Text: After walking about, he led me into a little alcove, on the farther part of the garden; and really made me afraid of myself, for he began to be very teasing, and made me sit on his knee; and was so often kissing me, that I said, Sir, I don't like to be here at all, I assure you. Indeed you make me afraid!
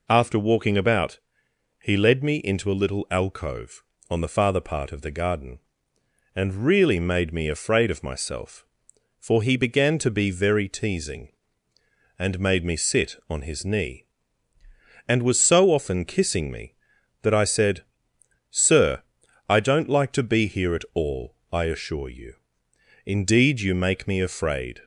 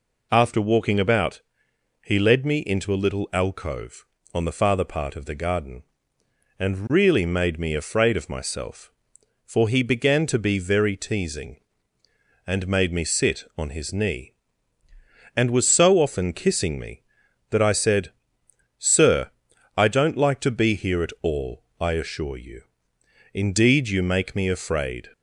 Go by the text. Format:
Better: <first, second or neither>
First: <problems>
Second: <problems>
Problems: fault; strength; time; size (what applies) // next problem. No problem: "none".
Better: neither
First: none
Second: none